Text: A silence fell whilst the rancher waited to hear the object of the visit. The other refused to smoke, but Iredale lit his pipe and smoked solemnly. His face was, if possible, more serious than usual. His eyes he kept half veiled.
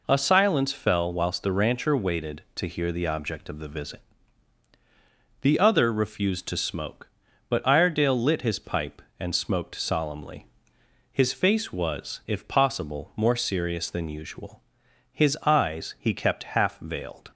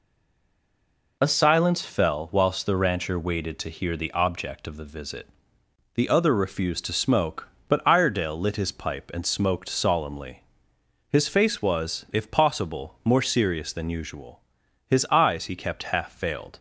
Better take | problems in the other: first | stays silent before the first word; noticeable; until 1.2 s; 1.2 s long

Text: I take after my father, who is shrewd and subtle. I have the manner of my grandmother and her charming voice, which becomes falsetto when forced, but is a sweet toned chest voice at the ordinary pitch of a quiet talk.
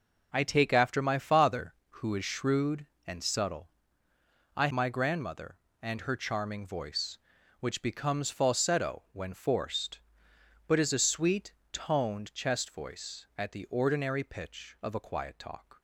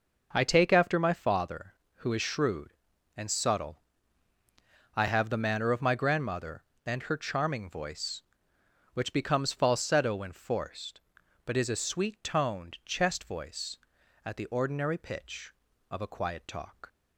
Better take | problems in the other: second | skips "have the manner of"; at 4.6 s // pauses between "sweet" and "toned"; slight; at 11.5 s; 0.20 s long

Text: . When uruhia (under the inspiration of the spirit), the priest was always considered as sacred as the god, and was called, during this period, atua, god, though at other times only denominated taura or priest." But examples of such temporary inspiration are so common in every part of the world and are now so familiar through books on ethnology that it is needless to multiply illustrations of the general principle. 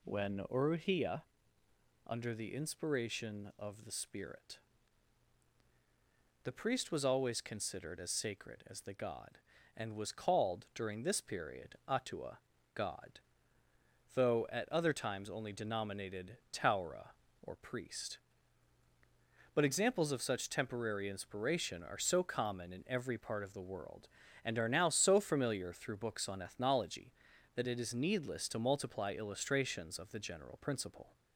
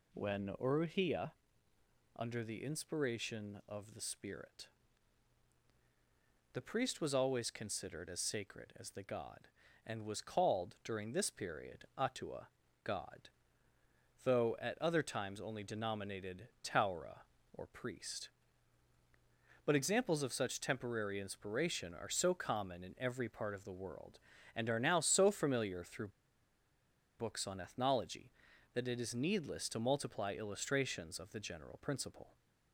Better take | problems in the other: first | pauses between "through" and "books"; at 26.0 s; 1.1 s long

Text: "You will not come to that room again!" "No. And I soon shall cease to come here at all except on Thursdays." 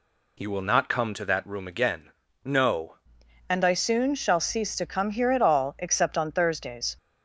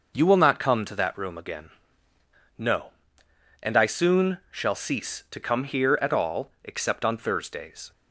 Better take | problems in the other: second | changes voice at "And"; from 3.5 s on; 3.4 s long

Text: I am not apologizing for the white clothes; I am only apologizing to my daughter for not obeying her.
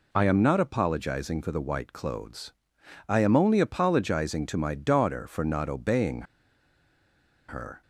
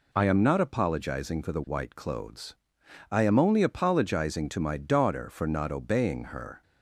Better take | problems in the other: second | pauses between "obeying" and "her"; strong; at 6.2 s; 1.2 s long

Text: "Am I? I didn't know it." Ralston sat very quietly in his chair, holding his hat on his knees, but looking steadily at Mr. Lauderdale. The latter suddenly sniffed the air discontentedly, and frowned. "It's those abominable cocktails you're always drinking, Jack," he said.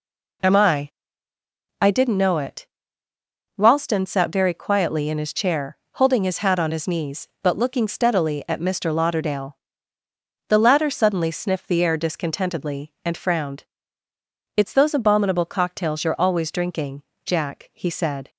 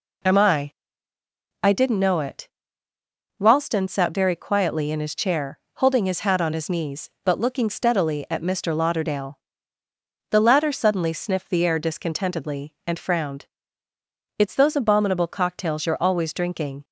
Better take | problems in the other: first | stops before "Jack he said"; at 16.8 s

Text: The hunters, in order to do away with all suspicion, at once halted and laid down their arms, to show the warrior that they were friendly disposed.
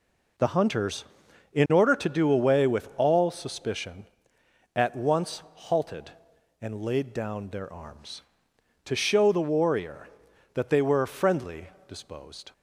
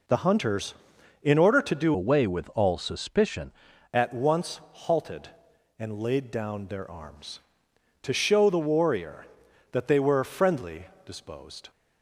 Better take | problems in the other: first | changes voice from "away" to "suspicion"; from 1.9 to 3.5 s; 1.6 s long // pauses between "friendly" and "disposed"; slight; at 10.8 s; 0.20 s long; slight in the first

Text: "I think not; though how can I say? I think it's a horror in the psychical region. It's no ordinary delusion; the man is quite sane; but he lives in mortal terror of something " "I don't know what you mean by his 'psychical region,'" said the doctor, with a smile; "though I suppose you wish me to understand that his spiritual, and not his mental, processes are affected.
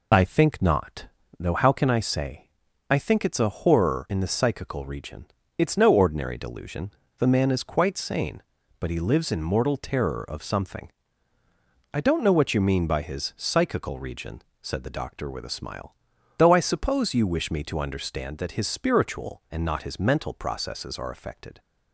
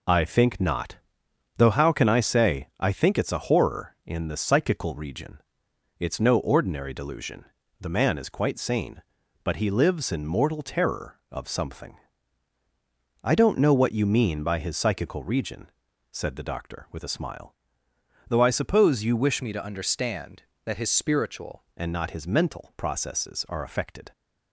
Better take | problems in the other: first | changes voice from "me" to "spiritual"; from 19.4 to 21.6 s; 2.2 s long

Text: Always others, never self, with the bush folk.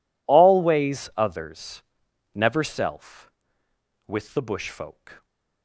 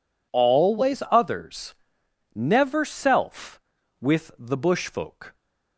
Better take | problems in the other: neither | none

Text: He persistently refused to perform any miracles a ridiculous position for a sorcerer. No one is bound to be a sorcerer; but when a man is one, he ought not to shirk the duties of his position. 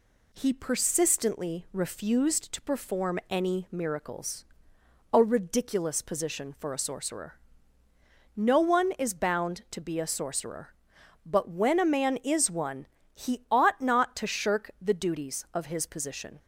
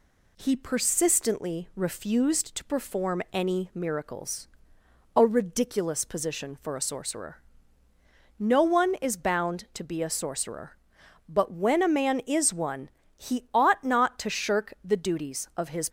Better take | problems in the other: first | pauses between "miracles" and "a"; noticeable; at 4.4 s; 0.70 s long; noticeable in the first // stops before "position"; at 15.8 s

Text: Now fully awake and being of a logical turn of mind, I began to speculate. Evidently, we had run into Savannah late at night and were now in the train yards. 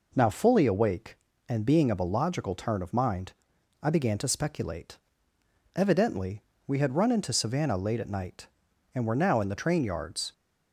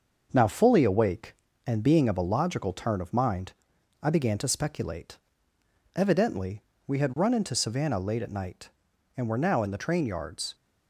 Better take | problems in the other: first | gets quieter; noticeable; throughout; 4 dB

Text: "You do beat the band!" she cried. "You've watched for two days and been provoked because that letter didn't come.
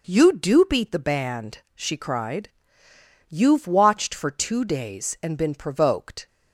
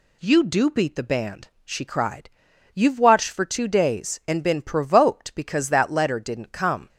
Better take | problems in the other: second | stops before "because that letter didn't come"; at 6.2 s

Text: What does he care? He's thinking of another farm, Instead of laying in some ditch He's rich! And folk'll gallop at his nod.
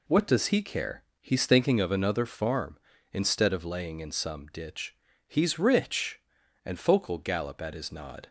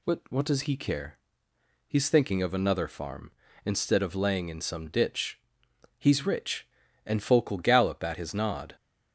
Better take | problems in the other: first | says "What" twice; at 0.3 s // pauses between "ditch" and "He's"; noticeable; at 5.3 s; 0.60 s long; slight in the first

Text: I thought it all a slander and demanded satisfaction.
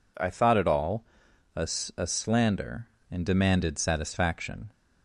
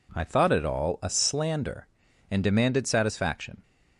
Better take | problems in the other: second | pauses between "all" and "a"; noticeable; at 1.0 s; 0.52 s long // says "a" twice; at 1.9 s

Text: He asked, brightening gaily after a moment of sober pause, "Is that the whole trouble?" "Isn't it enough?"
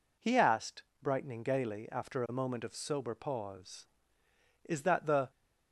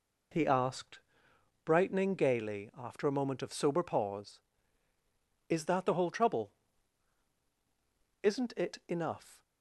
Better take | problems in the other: second | stops before "whole trouble Isn't it enough"; at 5.3 s

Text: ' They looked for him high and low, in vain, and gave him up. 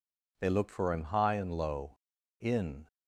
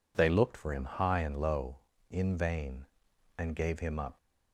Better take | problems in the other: second | stops before "vain and gave him up"; at 2.8 s

